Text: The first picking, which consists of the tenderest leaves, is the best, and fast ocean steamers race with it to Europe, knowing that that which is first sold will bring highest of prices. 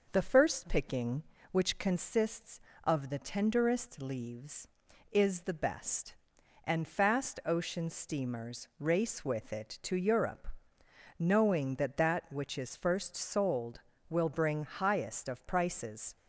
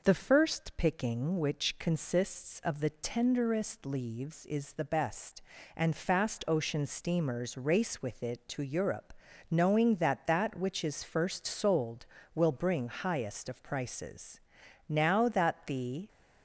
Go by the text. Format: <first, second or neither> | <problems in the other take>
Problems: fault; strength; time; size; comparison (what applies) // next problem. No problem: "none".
first | goes on to say "Now that the"; noticeable; from 14.8 s on; 1.2 s long